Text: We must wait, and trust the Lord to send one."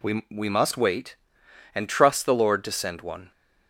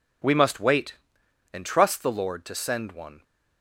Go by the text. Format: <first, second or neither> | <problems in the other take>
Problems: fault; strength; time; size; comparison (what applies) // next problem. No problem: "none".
second | says "We" twice; at 0.3 s